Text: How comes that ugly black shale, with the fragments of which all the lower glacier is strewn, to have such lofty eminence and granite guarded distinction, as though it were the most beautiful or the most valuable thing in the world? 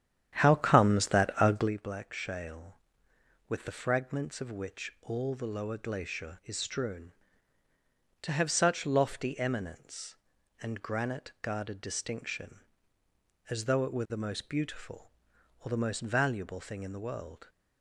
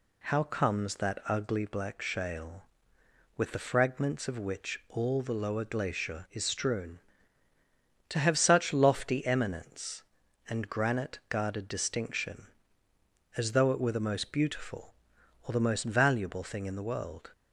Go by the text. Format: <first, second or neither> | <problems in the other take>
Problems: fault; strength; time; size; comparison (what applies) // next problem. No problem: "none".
second | starts louder than the rest; strong; until 1.7 s; 10 dB